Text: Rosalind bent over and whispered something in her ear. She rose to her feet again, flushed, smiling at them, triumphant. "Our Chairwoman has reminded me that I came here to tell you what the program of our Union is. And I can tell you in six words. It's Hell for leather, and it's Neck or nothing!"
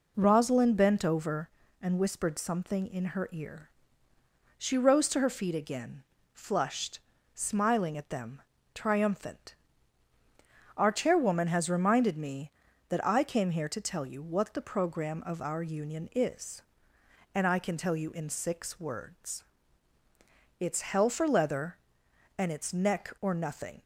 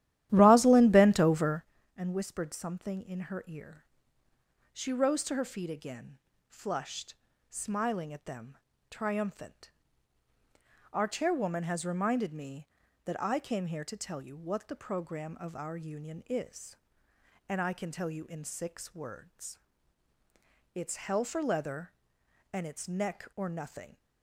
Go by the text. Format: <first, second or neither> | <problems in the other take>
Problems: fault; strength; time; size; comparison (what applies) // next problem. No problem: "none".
first | starts louder than the rest; strong; until 1.8 s; 13 dB